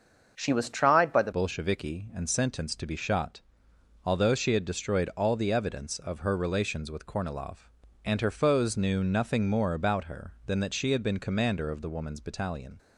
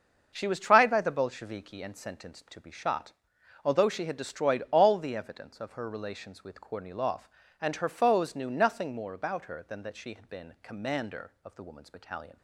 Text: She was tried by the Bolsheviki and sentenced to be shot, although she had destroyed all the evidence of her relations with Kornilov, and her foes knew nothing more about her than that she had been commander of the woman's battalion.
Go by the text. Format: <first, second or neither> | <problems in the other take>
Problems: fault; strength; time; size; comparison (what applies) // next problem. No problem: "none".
second | starts louder than the rest; until 1.3 s; 6.5 dB; also in the second // changes voice at "Bolsheviki"; from 1.3 s on; 11.4 s long